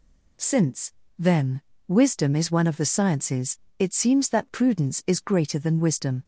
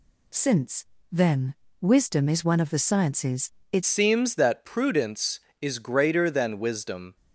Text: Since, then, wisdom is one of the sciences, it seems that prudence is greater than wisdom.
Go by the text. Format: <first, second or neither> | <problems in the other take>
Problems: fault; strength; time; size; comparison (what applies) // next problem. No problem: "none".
first | changes voice at "seems"; from 3.8 s on; 3.3 s long